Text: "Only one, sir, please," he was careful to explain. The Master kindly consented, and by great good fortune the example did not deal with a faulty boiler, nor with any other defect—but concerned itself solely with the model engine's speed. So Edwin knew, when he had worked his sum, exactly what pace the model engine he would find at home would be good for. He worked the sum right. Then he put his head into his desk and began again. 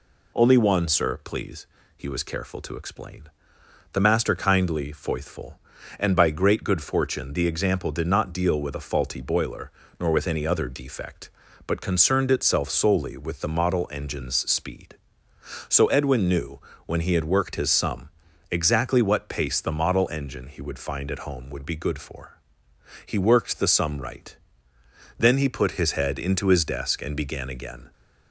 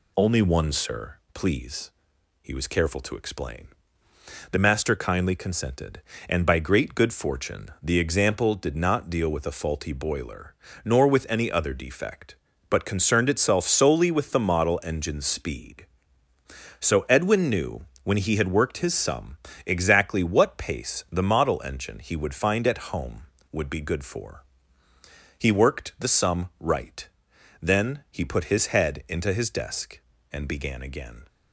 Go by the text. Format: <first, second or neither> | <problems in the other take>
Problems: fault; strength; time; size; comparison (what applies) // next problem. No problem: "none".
second | says "foithful" for "consented"; at 4.9 s